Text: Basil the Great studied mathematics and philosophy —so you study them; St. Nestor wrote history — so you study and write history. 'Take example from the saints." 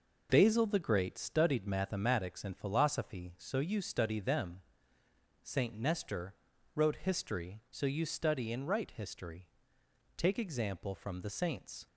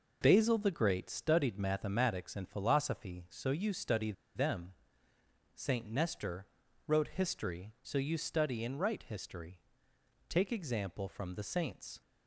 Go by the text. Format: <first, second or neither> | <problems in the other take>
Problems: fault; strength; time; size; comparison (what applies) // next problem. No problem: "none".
first | pauses between "study" and "them"; slight; at 4.1 s; 0.22 s long // pauses between "Nestor" and "wrote"; at 6.4 s; 0.38 s long; also in the first